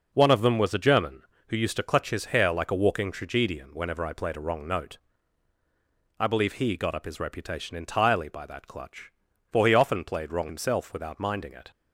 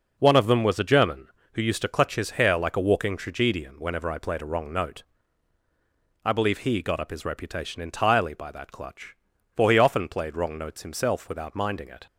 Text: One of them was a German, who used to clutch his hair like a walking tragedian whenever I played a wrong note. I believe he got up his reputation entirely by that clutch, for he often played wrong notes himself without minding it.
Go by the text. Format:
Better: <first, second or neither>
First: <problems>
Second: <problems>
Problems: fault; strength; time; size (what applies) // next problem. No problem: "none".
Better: second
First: skips "notes"; at 10.4 s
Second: none